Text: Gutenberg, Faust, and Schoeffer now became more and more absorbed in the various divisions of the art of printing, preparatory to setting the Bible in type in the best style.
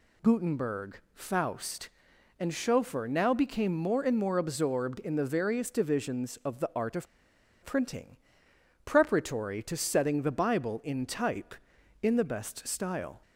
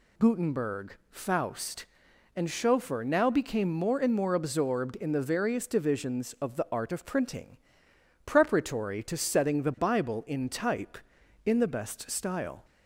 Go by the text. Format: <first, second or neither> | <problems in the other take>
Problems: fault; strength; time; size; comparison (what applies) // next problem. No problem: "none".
second | pauses between "of" and "printing"; noticeable; at 7.0 s; 0.58 s long